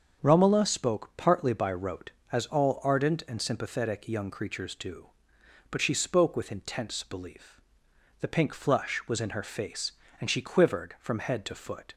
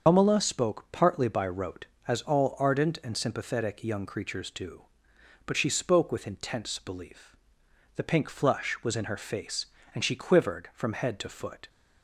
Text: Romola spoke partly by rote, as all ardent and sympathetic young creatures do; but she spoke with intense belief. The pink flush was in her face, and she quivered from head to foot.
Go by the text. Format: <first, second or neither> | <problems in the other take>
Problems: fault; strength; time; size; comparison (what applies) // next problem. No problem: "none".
first | loses the start of "Romola"; at 0.0 s; 100 ms // starts louder than the rest; until 1.0 s; 6.5 dB; also in the first